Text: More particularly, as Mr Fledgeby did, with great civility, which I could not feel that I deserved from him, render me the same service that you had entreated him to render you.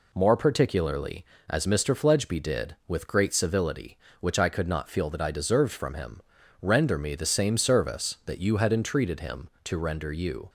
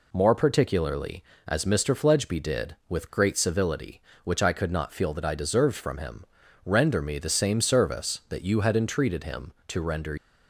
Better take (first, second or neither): first